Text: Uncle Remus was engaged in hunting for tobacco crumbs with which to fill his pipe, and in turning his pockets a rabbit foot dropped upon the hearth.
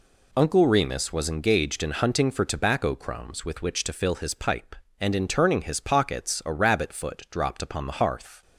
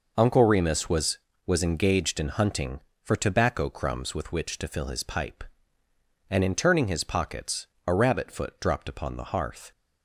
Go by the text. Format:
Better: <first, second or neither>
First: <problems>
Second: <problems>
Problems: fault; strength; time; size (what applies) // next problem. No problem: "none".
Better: first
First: none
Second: says "was" twice; at 1.4 s // pauses between "pockets" and "a"; slight; at 7.6 s; 0.20 s long